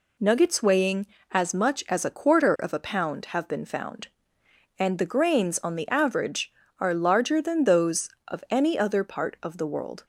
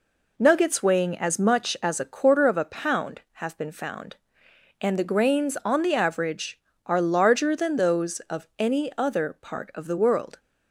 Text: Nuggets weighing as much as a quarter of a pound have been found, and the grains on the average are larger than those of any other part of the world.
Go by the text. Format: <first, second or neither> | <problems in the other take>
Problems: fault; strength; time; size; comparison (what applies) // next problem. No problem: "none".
neither | none